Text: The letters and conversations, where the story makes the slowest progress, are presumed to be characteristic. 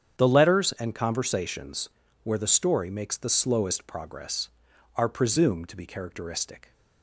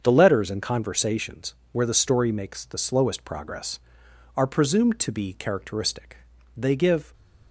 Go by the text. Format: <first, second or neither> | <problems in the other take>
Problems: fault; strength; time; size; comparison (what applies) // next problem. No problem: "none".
first | starts louder than the rest; until 1.0 s; 7 dB; strong in the first // goes on to say "They give"; from 6.5 s on; 0.56 s long